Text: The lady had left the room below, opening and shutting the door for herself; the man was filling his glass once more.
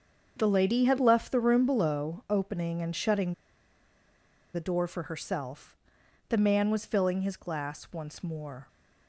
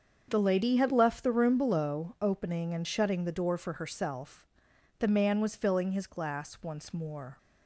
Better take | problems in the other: second | starts louder than the rest; until 1.3 s; 7 dB; also in the second // pauses between "shutting" and "the"; at 3.3 s; 1.2 s long

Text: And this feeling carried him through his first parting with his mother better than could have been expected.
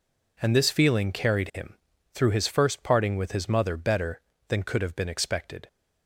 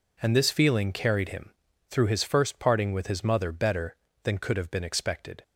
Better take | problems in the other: neither | pauses between "him" and "through"; the same in both

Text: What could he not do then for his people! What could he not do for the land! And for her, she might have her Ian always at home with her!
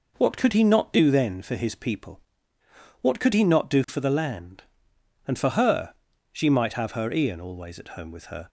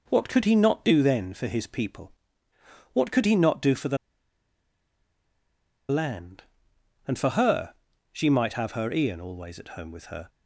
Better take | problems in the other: first | pauses between "the" and "land"; strong; at 3.9 s; 1.9 s long

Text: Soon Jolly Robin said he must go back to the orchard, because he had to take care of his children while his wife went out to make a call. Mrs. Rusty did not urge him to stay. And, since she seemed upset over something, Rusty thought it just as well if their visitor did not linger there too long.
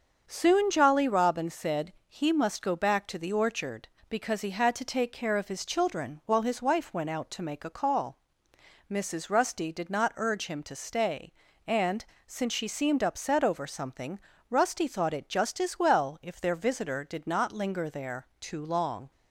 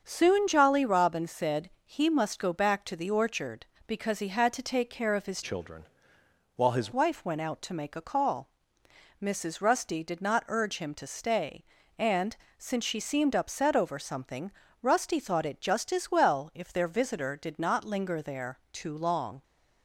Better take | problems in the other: first | starts louder than the rest; until 1.0 s; 6.5 dB; also in the first // pauses between "said" and "he"; slight; at 1.6 s; 0.16 s long; slight in the first // changes voice from "children" to "his"; from 5.4 to 6.9 s; 1.5 s long // pauses between "children" and "while"; noticeable; at 5.8 s; 0.72 s long

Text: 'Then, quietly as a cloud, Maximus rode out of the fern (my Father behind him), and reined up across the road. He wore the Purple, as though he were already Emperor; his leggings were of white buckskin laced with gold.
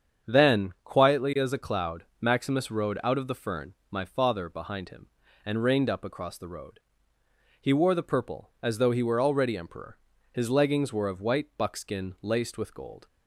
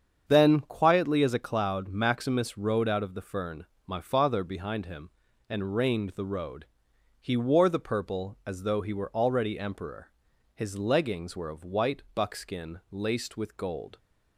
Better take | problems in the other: first | starts louder than the rest; strong; until 1.2 s; 7.5 dB; strong in the first // skips "up across"; at 6.1 s

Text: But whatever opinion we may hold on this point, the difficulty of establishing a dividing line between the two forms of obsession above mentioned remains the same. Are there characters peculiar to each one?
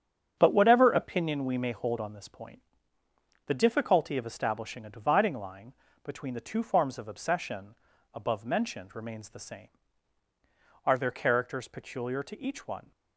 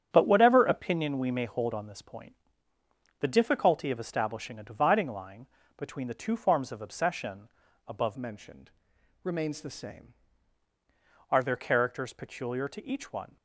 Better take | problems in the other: first | starts louder than the rest; strong; until 1.1 s; 8.5 dB; strong in the first // pauses between "line" and "between"; slight; at 5.4 s; 0.32 s long; slight in the first // pauses between "obsession" and "above"; at 7.4 s; 0.40 s long; also in the first // changes voice from "mentioned" to "same"; from 8.1 to 10.1 s; 2.0 s long // pauses between "mentioned" and "remains"; noticeable; at 8.6 s; 0.52 s long

